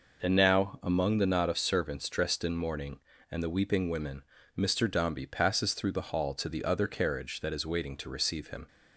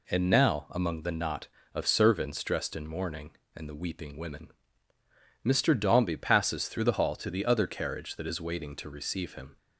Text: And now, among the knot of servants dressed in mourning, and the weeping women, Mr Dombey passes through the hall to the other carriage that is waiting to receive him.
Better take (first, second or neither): neither